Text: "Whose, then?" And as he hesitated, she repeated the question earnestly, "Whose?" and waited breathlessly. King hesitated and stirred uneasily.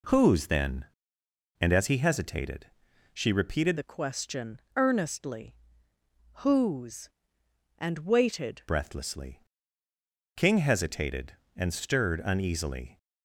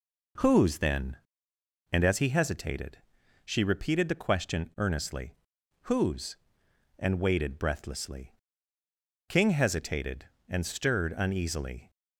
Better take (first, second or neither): second